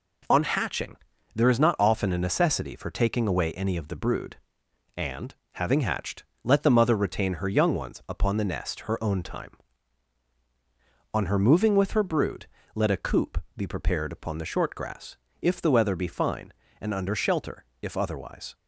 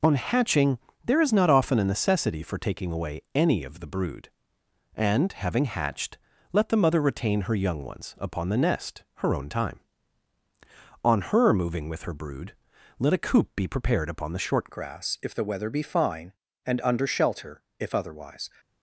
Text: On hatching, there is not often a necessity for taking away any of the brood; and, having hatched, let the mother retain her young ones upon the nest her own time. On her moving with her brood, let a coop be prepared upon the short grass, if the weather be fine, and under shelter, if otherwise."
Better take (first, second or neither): first